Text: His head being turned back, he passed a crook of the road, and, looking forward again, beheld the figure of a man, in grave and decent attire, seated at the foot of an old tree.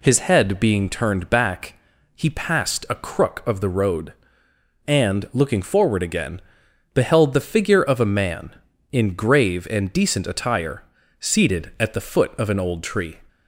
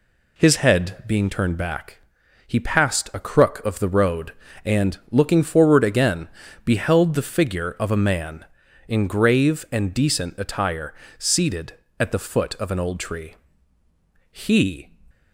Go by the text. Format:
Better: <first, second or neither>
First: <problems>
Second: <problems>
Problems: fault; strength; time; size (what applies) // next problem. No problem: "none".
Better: first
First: none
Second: goes on to say "He"; from 14.3 s on; 0.60 s long